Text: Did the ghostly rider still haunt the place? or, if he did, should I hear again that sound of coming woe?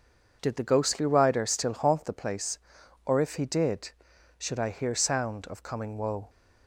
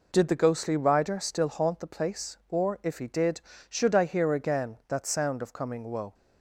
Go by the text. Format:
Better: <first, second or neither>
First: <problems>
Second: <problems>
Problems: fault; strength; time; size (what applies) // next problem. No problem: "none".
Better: second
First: skips "again that"; at 4.9 s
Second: none